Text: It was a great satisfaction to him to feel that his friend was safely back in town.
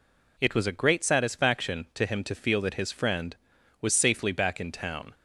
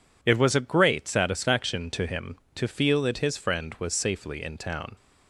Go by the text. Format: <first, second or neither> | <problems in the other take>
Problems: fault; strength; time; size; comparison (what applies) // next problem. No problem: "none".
first | skips "back"; at 4.4 s